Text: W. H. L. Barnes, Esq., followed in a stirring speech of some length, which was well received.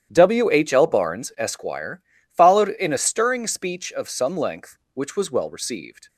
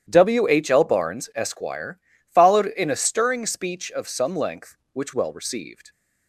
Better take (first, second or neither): first